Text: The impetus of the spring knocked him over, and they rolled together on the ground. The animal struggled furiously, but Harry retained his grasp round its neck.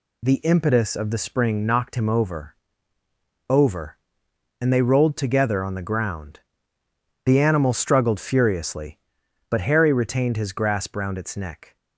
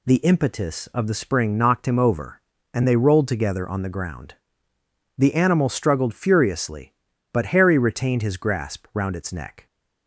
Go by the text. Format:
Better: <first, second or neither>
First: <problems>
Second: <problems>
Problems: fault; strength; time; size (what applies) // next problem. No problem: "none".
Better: second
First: says "over" twice; at 3.4 s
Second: none